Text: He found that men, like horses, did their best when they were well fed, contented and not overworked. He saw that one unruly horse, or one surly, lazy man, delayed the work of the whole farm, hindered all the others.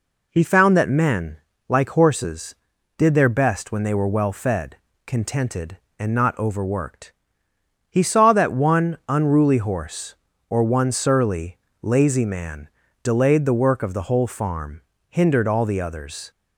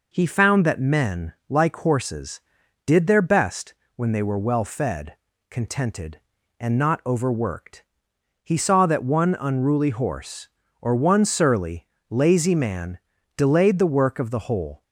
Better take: first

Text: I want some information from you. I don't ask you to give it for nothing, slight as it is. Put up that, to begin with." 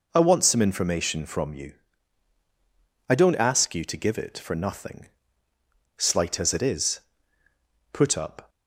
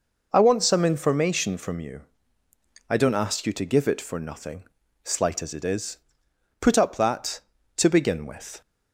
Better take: second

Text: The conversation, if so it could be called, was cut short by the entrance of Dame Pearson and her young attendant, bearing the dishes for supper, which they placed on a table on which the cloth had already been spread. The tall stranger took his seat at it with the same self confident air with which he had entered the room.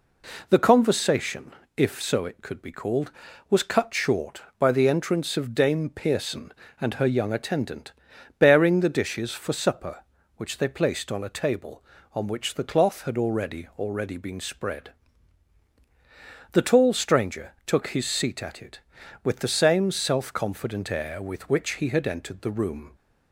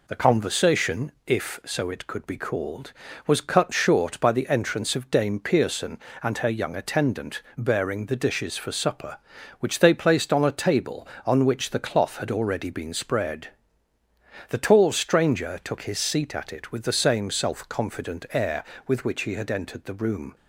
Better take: second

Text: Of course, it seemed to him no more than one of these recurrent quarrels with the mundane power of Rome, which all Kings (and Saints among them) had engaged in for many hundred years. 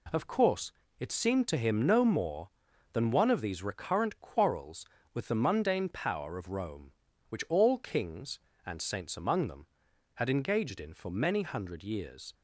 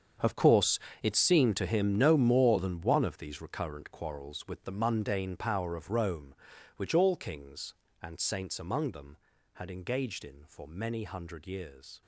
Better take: first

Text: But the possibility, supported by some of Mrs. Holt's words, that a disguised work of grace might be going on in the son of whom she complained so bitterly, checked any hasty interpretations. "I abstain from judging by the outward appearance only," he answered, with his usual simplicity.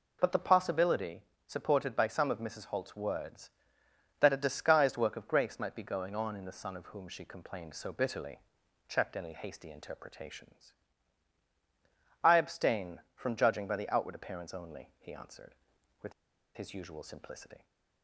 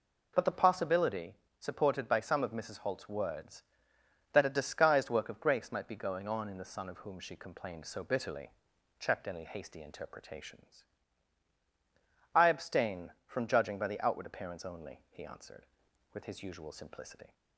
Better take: second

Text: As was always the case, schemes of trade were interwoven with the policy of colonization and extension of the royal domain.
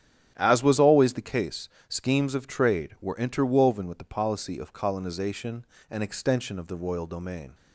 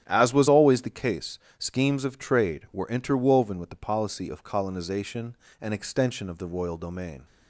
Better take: neither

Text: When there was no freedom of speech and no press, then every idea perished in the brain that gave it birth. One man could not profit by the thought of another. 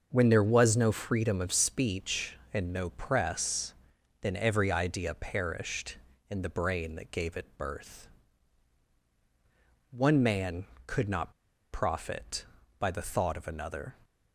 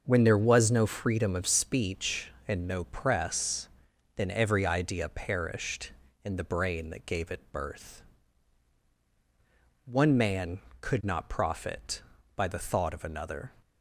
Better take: second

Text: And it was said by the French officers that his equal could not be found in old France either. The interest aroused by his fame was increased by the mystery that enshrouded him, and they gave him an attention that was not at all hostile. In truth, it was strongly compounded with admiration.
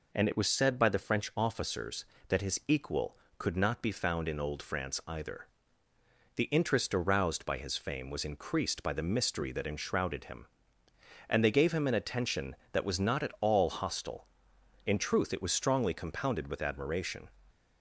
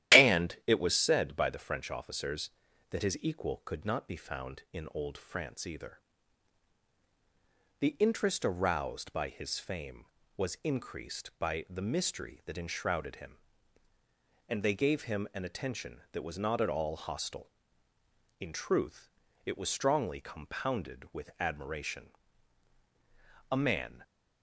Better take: first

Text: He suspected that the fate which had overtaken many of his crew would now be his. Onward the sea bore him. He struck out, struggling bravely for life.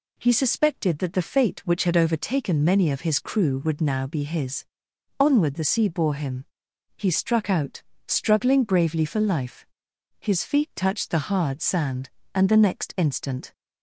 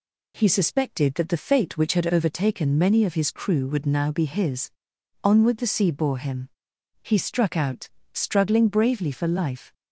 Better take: second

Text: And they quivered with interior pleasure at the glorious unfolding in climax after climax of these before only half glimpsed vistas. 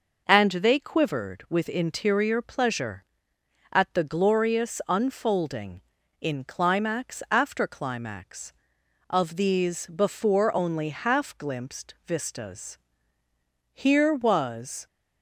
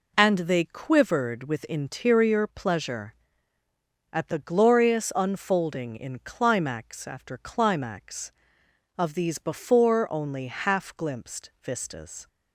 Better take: second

